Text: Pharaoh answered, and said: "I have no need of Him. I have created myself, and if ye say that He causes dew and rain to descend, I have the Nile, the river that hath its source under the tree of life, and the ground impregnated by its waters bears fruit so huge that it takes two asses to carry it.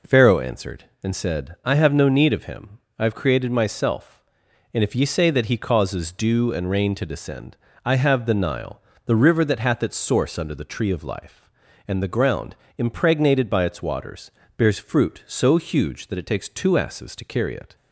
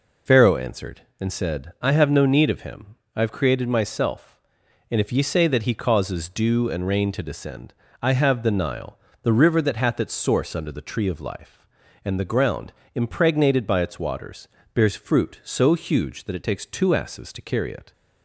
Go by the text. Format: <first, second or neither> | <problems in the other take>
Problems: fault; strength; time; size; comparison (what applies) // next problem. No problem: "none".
first | loses the start of "Pharaoh"; at 0.2 s; 45 ms // pauses between "ground" and "impregnated"; slight; at 12.7 s; 0.22 s long; slight in the first // pauses between "waters" and "bears"; slight; at 14.4 s; 0.28 s long; slight in the first